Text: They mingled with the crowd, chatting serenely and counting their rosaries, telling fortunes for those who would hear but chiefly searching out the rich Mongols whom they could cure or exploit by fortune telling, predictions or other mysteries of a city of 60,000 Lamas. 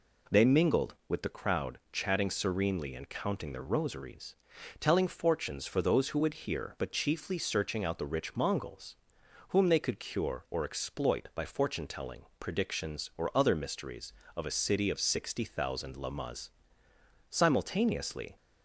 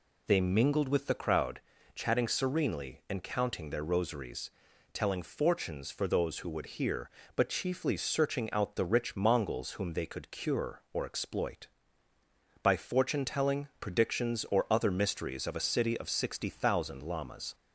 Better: second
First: pauses between "Mongols" and "whom"; noticeable; at 8.9 s; 0.54 s long // goes on to say "Simultaneously"; noticeable; from 17.2 s on; 1.0 s long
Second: none

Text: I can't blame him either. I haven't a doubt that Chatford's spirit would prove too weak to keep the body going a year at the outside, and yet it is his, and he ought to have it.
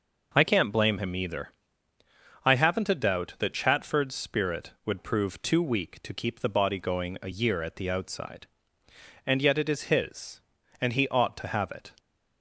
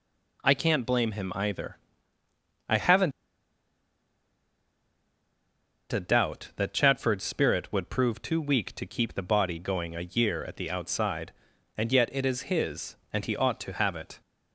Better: first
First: none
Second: pauses between "haven't" and "a"; strong; at 3.1 s; 2.8 s long

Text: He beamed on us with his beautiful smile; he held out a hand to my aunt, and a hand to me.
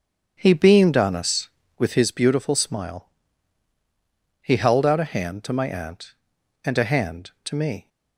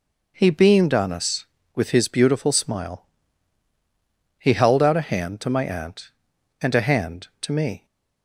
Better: second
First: starts louder than the rest; strong; until 2.1 s; 8.5 dB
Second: none

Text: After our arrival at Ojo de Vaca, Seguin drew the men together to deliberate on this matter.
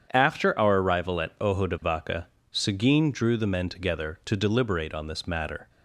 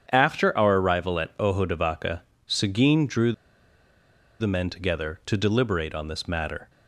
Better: first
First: starts louder than the rest; strong; until 1.1 s; 8 dB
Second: starts louder than the rest; strong; until 1.1 s; 8 dB // pauses between "drew" and "the"; at 3.3 s; 1.0 s long

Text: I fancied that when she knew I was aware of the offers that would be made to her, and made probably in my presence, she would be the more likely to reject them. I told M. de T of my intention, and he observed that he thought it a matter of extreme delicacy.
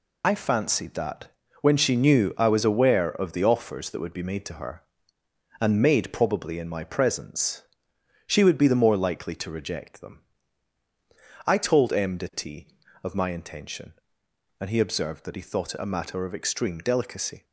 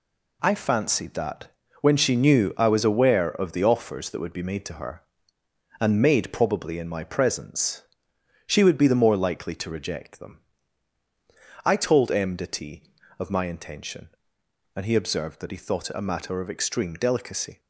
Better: second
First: loses the start of "I"; at 0.2 s; 30 ms // pauses between "that" and "when"; slight; at 1.2 s; 0.32 s long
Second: pauses between "that" and "when"; slight; at 1.4 s; 0.32 s long

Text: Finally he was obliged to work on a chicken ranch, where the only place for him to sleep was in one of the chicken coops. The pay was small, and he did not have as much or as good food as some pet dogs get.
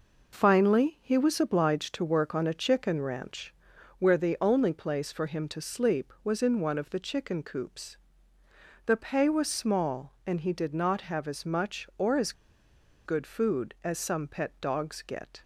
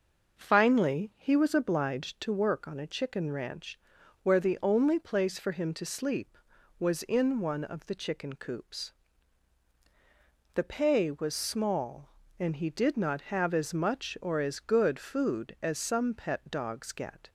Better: second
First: pauses between "as" and "good"; noticeable; at 12.3 s; 0.73 s long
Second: none

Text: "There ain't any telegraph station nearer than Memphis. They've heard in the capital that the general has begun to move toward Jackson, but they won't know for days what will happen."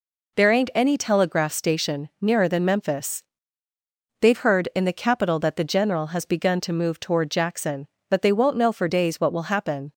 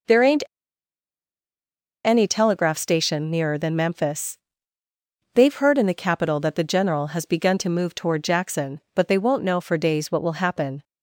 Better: first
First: none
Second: pauses between "ain't" and "any"; strong; at 0.4 s; 1.6 s long

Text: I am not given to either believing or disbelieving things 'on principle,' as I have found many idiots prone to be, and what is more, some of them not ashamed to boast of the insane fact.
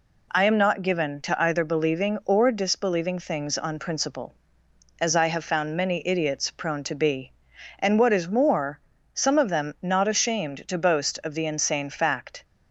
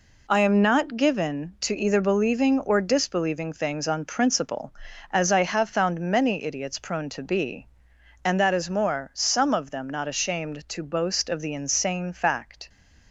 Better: first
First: none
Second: says "that" for "what"; at 8.3 s

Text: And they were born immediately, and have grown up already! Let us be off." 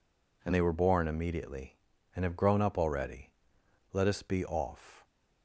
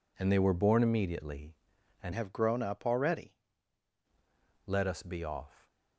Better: first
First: none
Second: changes voice from "have" to "already"; from 2.1 to 3.3 s; 1.2 s long

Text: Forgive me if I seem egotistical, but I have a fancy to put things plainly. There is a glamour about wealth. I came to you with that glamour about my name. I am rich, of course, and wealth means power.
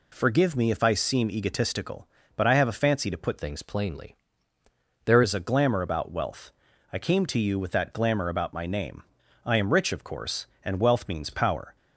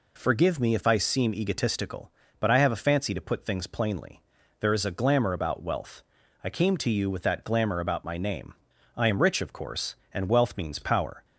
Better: second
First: changes voice from "things" to "There"; from 3.3 to 5.2 s; 1.9 s long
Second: none

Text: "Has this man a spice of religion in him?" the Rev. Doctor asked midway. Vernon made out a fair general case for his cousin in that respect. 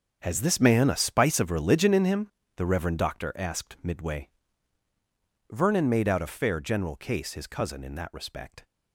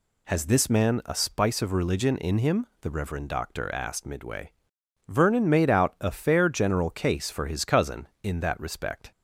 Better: second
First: starts louder than the rest; until 1.2 s; 6.5 dB // skips "for"; at 7.3 s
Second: none

